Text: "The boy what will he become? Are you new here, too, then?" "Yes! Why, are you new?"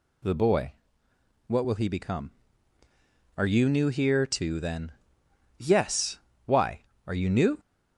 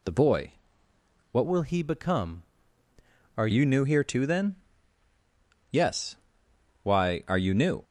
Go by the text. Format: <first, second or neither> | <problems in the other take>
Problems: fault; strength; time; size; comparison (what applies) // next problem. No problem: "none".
first | pauses between "boy" and "what"; noticeable; at 0.5 s; 0.80 s long; noticeable in the first // changes voice from "will" to "Are"; from 1.4 to 3.4 s; 2.0 s long